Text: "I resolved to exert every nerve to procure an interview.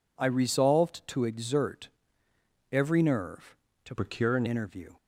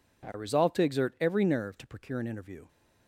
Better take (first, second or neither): second